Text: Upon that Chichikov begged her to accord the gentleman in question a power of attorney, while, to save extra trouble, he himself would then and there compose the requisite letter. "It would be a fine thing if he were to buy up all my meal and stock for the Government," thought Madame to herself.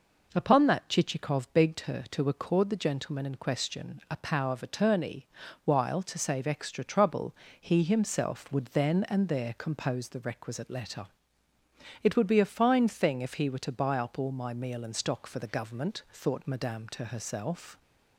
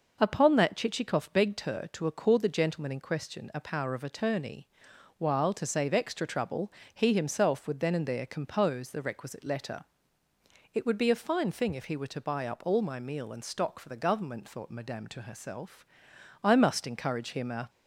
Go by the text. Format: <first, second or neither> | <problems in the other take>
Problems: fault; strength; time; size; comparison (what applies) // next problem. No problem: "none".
first | goes on to say "I must encourage him a"; noticeable; from 16.4 s on; 1.2 s long